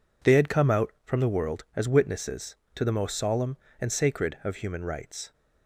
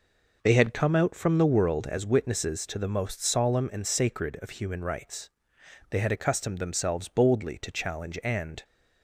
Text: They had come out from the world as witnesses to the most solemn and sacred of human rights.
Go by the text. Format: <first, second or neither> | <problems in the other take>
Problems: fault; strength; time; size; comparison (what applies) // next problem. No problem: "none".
first | goes on to say "They had accustomed themselves boldly to challenge and"; strong; from 5.8 s on; 2.7 s long